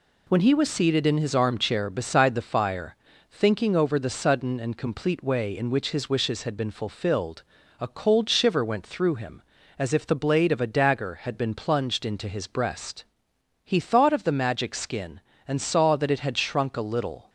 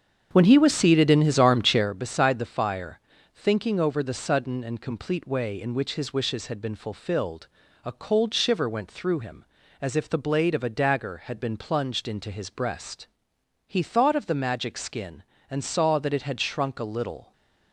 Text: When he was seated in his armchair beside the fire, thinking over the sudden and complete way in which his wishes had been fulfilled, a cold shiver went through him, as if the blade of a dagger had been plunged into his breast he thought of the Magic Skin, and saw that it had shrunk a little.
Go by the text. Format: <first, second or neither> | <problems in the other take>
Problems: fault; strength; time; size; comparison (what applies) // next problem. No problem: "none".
first | starts louder than the rest; strong; until 1.9 s; 7.5 dB // pauses between "breast" and "he"; noticeable; at 13.0 s; 0.60 s long; noticeable in the first